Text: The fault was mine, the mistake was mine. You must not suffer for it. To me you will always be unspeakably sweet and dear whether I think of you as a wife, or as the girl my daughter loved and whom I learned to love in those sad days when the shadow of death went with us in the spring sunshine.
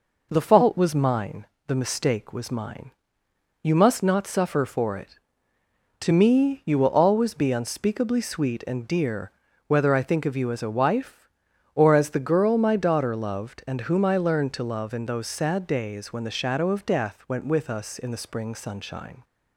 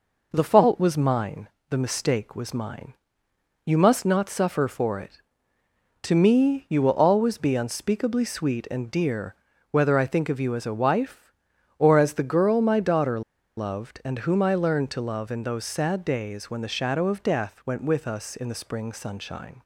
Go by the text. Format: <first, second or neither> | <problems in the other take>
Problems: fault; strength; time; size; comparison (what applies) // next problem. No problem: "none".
first | pauses between "dear" and "whether"; at 9.3 s; 0.38 s long; also in the first // pauses between "daughter" and "loved"; at 13.2 s; 0.36 s long